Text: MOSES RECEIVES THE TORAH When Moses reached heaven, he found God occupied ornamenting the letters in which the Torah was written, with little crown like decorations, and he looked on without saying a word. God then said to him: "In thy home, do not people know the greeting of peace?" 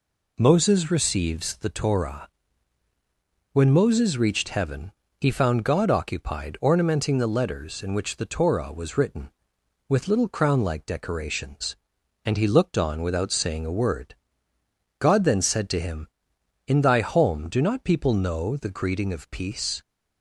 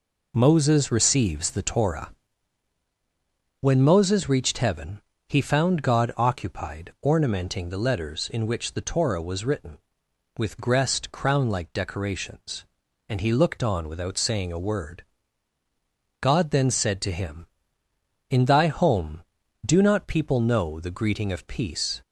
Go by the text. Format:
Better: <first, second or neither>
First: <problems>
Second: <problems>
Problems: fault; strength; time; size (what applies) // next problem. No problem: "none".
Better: first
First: pauses between "TORAH" and "When"; at 2.2 s; 1.2 s long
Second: pauses between "TORAH" and "When"; strong; at 2.0 s; 1.5 s long // says "gressed" for "little"; at 10.5 s